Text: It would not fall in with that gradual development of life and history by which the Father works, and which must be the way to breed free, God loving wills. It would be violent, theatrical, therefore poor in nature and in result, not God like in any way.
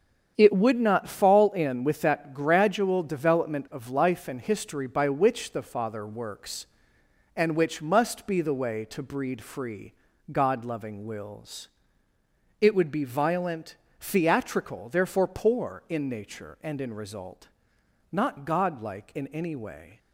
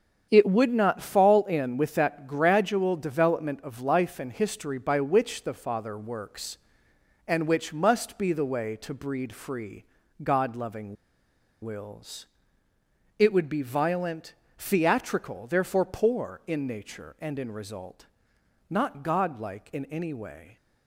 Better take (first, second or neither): first